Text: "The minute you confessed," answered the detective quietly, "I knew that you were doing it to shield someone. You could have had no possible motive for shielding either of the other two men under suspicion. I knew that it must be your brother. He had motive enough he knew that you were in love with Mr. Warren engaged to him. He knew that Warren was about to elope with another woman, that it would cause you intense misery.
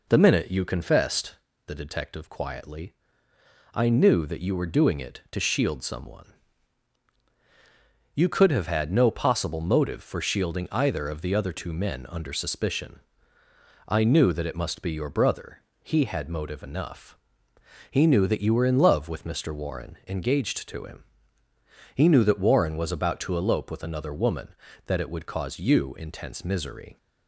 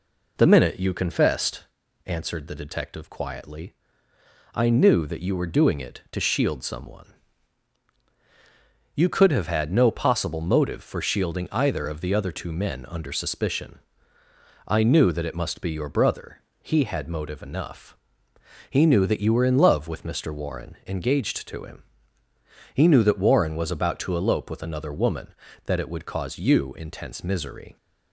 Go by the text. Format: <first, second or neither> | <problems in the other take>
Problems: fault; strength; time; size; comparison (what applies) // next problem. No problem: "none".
second | skips "answered"; at 1.5 s // pauses between "enough" and "he"; noticeable; at 17.1 s; 0.74 s long; noticeable in the second